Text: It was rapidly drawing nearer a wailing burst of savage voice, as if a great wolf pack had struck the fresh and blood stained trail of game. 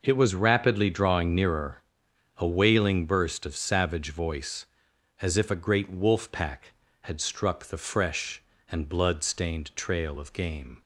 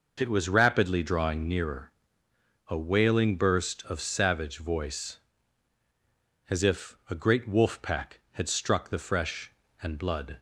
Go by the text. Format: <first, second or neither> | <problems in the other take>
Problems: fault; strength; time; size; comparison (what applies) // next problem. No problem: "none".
first | pauses between "nearer" and "a"; noticeable; at 1.9 s; 0.74 s long; noticeable in the first // stops before "stained trail of game"; at 10.3 s